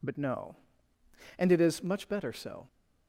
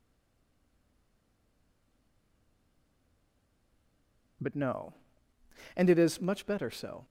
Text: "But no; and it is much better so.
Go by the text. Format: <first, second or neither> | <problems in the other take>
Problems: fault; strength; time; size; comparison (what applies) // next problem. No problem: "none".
first | stays silent before the first word; strong; until 4.4 s; 4.4 s long